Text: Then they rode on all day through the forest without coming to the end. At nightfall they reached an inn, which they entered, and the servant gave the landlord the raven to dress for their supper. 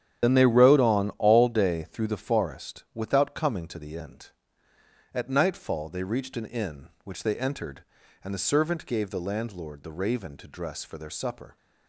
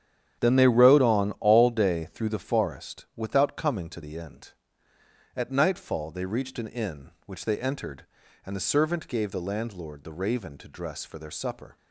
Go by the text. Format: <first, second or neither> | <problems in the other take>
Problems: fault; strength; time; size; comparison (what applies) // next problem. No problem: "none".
second | loses the start of "Then"; at 0.2 s; 40 ms // starts louder than the rest; strong; until 1.3 s; 10 dB; strong in the second